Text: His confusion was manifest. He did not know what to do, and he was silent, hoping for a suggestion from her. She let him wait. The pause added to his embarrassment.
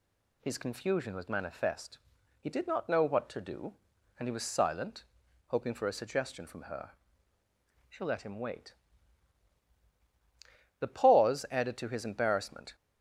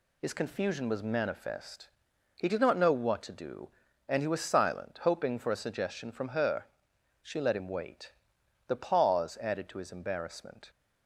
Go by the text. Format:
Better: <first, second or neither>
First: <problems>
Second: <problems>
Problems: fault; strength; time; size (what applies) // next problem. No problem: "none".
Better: neither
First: none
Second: none